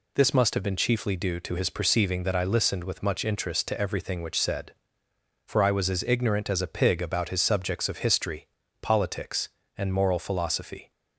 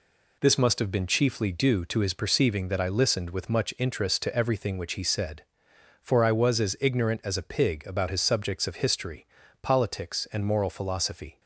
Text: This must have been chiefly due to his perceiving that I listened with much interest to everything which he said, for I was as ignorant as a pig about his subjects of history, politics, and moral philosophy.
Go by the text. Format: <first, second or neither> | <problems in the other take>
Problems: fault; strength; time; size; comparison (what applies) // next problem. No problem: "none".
second | skips "he"; at 4.4 s